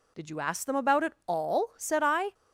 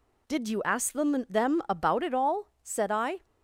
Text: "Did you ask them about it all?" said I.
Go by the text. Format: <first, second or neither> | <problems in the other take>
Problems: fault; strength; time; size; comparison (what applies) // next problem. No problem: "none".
first | says "them" twice; at 1.2 s